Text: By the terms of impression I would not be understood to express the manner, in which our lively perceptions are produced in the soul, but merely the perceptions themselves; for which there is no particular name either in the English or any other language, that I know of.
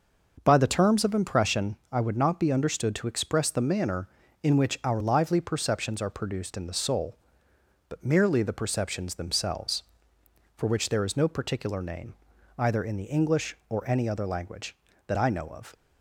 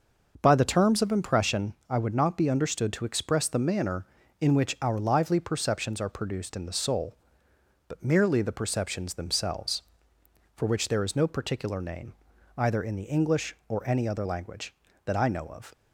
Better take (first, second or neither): neither